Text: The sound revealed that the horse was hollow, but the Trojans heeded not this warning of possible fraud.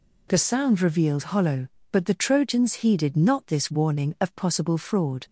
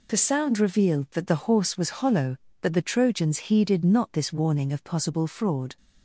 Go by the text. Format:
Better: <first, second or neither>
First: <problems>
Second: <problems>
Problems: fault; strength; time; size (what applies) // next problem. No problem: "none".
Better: second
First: skips "that the horse was"; at 1.3 s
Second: none